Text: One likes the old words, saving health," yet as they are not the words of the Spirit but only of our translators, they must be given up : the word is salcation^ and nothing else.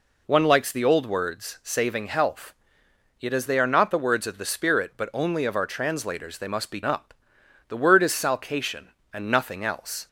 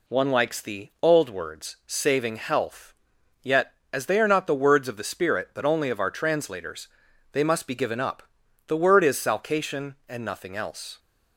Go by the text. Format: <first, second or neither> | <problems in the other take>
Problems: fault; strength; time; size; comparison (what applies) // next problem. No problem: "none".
second | skips "given"; at 6.8 s